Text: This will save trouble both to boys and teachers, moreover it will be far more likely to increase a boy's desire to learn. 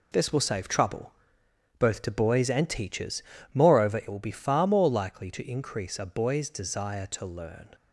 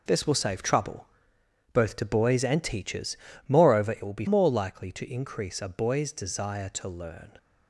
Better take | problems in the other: first | pauses between "trouble" and "both"; noticeable; at 1.0 s; 0.68 s long; noticeable in the first // skips "far"; at 4.2 s

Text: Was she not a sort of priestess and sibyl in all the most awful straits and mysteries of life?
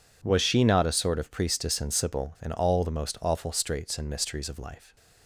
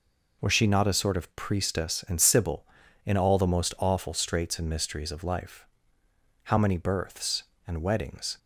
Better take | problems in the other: first | goes on to say "How many births and weddings"; strong; from 6.4 s on; 1.9 s long

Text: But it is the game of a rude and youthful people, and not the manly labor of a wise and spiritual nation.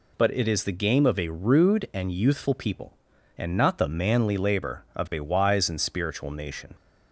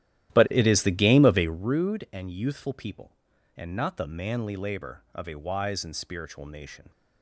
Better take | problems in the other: first | starts louder than the rest; strong; until 1.7 s; 13 dB

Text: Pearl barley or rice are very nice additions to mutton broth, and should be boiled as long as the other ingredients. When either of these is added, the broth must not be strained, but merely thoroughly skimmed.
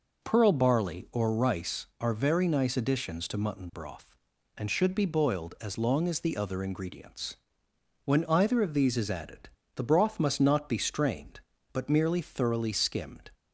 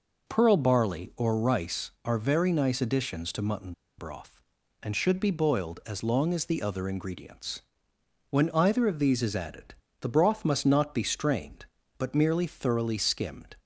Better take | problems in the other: first | pauses between "mutton" and "broth"; slight; at 3.7 s; 0.26 s long

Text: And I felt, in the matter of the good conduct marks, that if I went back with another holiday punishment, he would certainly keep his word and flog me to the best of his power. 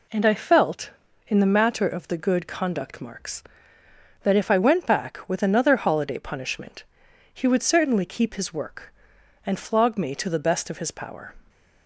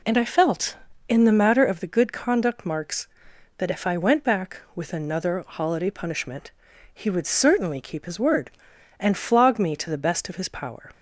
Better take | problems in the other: second | says "work" for "word"; at 8.5 s

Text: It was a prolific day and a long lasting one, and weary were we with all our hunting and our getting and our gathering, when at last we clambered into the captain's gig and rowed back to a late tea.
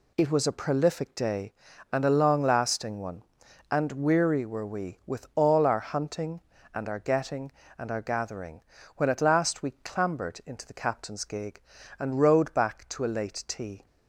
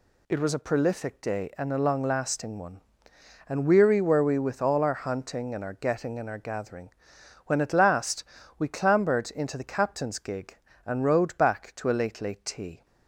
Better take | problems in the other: first | pauses between "last" and "we"; slight; at 8.2 s; 0.34 s long // says "late" twice; at 12.2 s

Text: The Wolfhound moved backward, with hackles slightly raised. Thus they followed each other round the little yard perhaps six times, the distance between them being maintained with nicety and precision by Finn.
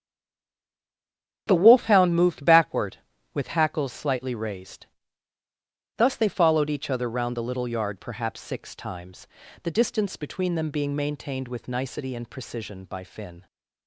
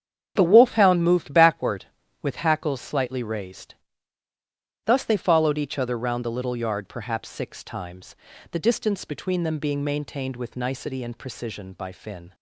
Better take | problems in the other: second | stays silent before the first word; noticeable; until 1.4 s; 1.4 s long // starts louder than the rest; strong; until 2.4 s; 8 dB; strong in the second

